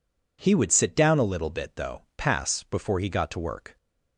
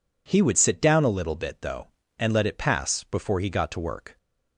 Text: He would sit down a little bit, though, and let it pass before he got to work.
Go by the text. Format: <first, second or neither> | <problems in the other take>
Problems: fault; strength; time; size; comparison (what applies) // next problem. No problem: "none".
second | skips "and let it"; at 2.1 s